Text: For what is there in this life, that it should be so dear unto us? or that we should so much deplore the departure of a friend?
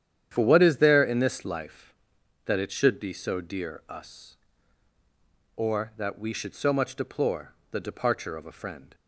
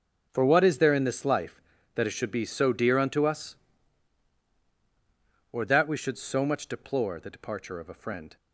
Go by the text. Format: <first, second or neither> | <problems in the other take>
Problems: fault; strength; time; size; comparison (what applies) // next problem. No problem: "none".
second | starts louder than the rest; strong; until 1.3 s; 9.5 dB; also in the second // skips "unto"; at 3.8 s // pauses between "deplore" and "the"; slight; at 7.5 s; 0.18 s long